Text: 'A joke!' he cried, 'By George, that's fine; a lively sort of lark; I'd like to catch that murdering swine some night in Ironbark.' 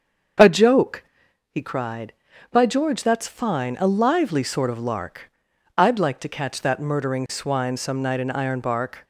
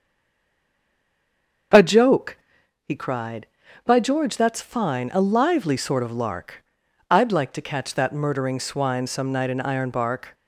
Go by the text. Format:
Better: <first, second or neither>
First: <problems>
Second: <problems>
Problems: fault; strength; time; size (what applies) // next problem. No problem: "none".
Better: first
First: starts louder than the rest; until 1.8 s; 6.5 dB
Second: stays silent before the first word; noticeable; until 1.7 s; 1.7 s long // starts louder than the rest; noticeable; until 3.2 s; 6 dB